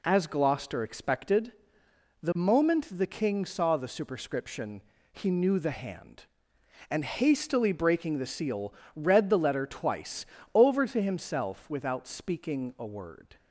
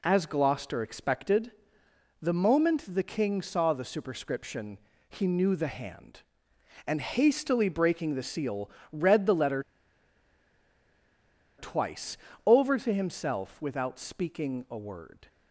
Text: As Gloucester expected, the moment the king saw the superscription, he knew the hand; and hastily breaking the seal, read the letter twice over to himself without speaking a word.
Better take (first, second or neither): first